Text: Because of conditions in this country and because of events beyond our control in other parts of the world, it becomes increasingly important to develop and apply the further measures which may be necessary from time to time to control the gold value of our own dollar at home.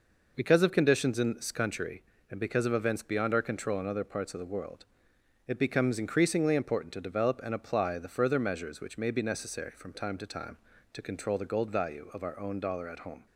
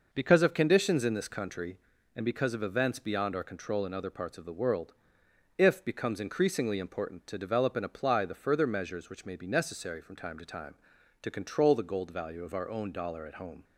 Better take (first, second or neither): first